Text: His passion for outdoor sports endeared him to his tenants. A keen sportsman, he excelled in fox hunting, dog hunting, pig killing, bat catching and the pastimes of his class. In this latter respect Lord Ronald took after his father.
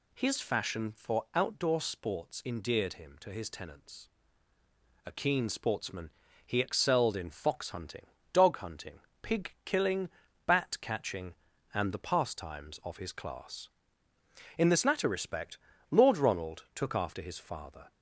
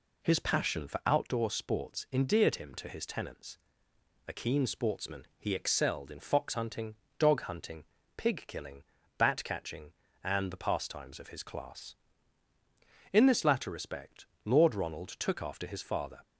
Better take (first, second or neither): second